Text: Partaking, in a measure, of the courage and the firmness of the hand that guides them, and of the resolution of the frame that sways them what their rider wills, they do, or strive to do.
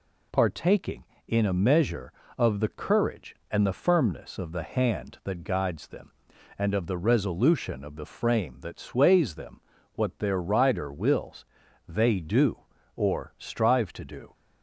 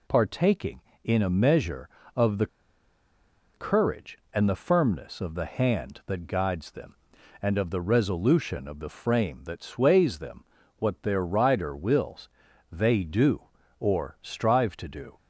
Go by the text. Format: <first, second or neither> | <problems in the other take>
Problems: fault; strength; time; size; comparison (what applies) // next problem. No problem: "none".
first | pauses between "the" and "courage"; at 2.4 s; 1.0 s long // pauses between "them" and "what"; slight; at 10.4 s; 0.34 s long; slight in the first